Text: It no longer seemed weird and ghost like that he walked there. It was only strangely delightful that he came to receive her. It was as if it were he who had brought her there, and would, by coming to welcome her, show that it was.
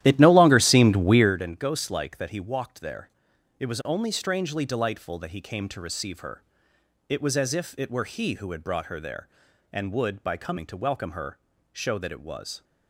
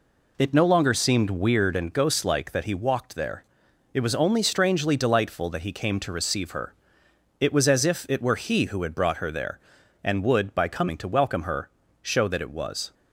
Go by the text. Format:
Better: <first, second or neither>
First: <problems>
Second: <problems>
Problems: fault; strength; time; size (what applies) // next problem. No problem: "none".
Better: second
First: starts louder than the rest; strong; until 1.3 s; 13 dB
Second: none